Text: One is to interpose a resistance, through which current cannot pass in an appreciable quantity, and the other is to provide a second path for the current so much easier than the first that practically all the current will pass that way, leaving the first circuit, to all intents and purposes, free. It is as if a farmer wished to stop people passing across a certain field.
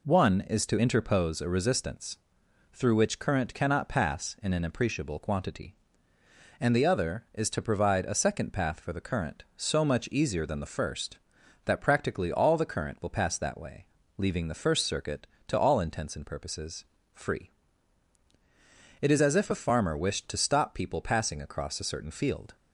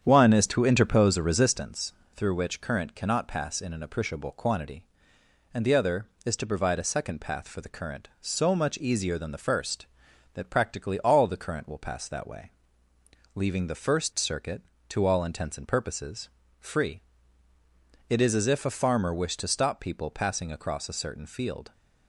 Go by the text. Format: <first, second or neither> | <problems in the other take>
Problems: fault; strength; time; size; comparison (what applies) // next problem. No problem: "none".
first | starts louder than the rest; strong; until 1.7 s; 8.5 dB